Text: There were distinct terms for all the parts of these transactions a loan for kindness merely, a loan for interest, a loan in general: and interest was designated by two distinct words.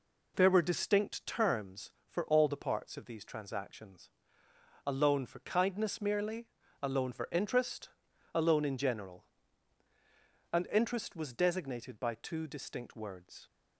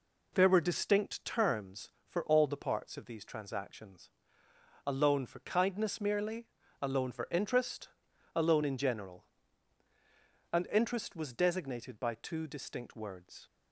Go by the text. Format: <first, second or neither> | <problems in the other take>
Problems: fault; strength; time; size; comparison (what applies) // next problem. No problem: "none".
neither | pauses between "transactions" and "a"; noticeable; the same in both